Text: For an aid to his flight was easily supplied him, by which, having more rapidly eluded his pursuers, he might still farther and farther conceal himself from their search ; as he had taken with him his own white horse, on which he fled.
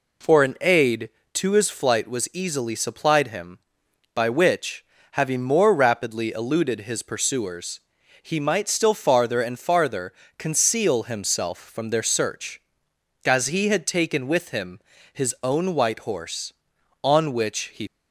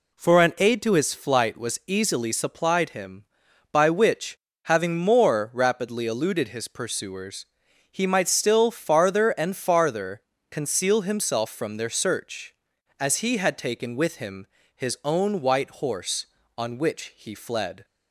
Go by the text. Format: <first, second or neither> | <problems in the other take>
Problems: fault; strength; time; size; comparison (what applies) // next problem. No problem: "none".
second | pauses between "farther" and "conceal"; slight; at 10.1 s; 0.24 s long; slight in the second // pauses between "him" and "his"; slight; at 14.7 s; 0.32 s long; slight in the second // stops before "fled"; at 17.8 s